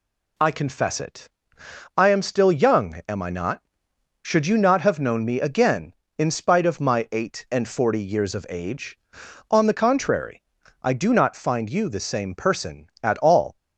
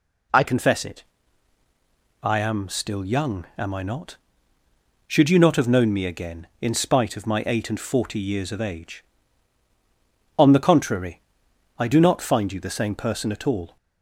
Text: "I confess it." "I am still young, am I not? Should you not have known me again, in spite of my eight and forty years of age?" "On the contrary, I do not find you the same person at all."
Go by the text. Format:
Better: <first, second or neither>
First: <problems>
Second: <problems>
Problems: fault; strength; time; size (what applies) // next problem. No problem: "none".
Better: first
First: none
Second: changes voice at "confess"; from 0.4 s on; 13.3 s long